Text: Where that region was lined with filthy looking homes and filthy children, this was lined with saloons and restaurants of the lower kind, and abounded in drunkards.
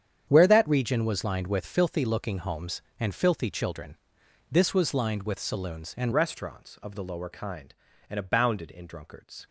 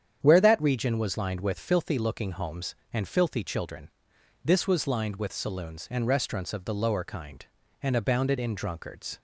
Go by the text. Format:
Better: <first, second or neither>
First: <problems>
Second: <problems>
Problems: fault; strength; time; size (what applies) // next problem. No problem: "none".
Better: second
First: starts louder than the rest; strong; until 1.2 s; 8.5 dB // changes voice at "restaurants"; from 6.1 s on; 3.3 s long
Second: starts louder than the rest; strong; until 1.2 s; 8.5 dB